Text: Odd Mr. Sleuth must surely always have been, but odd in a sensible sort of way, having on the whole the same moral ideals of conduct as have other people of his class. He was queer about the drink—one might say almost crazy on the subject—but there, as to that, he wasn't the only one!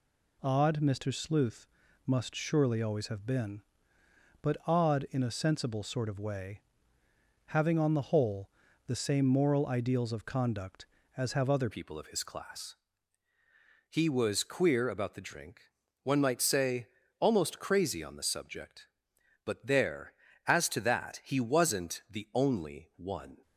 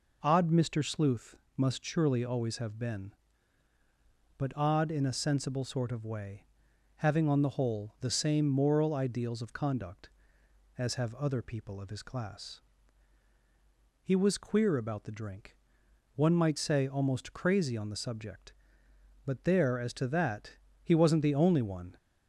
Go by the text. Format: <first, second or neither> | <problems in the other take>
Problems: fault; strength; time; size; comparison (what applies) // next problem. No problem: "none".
second | pauses between "Sleuth" and "must"; at 1.6 s; 0.38 s long; slight in the second // pauses between "whole" and "the"; at 8.4 s; 0.38 s long // changes voice at "people"; from 11.6 s on; 11.8 s long // pauses between "say" and "almost"; slight; at 16.8 s; 0.32 s long